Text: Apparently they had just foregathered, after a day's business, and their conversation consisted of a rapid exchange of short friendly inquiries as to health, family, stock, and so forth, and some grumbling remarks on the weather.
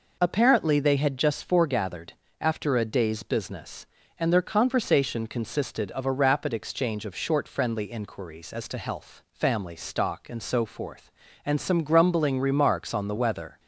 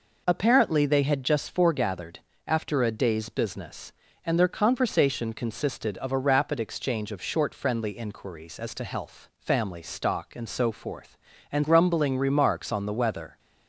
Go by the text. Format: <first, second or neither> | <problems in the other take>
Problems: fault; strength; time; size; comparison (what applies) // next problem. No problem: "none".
first | skips "some"; at 11.6 s